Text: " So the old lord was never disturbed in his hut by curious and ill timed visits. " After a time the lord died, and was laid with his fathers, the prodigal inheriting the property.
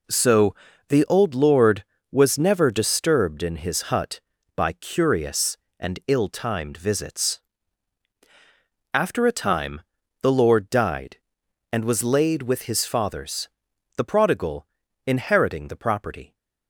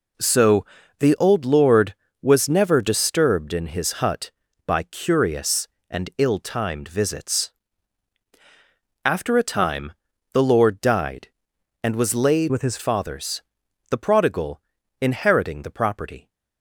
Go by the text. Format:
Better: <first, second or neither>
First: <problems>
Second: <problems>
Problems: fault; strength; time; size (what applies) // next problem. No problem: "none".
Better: first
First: pauses between "So" and "the"; slight; at 0.5 s; 0.34 s long // pauses between "time" and "the"; at 9.7 s; 0.40 s long // pauses between "prodigal" and "inheriting"; at 14.6 s; 0.40 s long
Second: pauses between "So" and "the"; slight; at 0.6 s; 0.34 s long // pauses between "time" and "the"; at 9.9 s; 0.40 s long // changes voice from "with" to "his"; from 12.4 to 12.7 s; 0.3 s long // pauses between "prodigal" and "inheriting"; at 14.6 s; 0.40 s long